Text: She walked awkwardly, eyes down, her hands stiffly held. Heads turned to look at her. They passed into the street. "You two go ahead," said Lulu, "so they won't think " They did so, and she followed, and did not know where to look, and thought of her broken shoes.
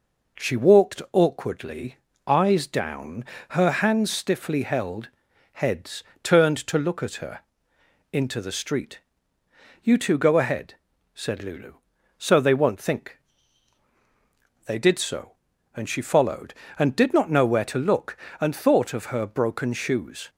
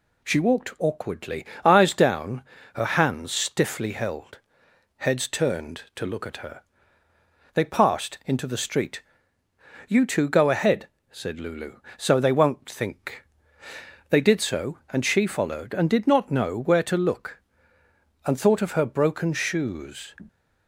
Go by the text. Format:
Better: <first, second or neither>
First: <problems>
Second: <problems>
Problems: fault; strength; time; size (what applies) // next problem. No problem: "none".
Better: second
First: pauses between "Heads" and "turned"; slight; at 6.0 s; 0.20 s long // skips "They passed"; at 7.7 s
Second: none